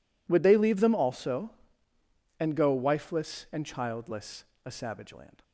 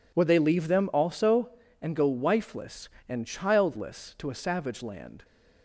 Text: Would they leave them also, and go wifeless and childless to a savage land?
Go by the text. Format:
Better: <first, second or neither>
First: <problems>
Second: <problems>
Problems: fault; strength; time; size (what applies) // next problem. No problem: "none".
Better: second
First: skips "to"; at 4.5 s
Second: none